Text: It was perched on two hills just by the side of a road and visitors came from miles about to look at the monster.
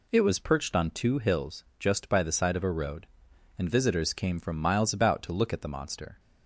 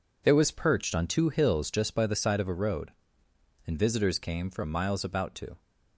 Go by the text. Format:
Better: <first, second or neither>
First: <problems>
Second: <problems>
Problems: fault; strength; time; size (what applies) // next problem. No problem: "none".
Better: first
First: none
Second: stops before "look at the monster"; at 5.5 s